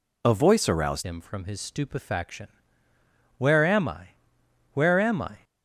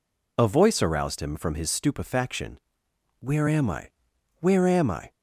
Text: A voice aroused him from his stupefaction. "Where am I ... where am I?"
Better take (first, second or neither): second